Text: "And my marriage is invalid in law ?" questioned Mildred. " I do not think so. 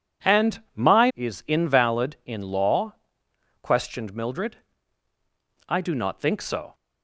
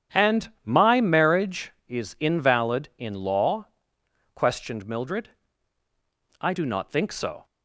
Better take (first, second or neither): second